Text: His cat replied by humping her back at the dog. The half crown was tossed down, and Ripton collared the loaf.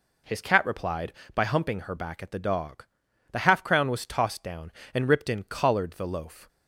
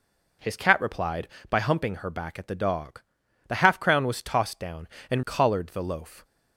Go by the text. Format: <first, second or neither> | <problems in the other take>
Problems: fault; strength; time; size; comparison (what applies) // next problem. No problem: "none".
first | skips "Ripton"; at 5.2 s